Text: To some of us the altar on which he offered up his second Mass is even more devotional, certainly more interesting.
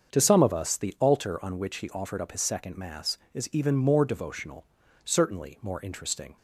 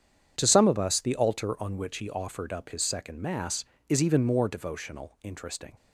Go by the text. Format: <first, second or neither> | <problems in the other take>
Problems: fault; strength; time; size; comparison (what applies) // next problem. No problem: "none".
first | starts louder than the rest; strong; until 1.3 s; 8 dB; also in the first // skips "certainly more"; at 5.1 s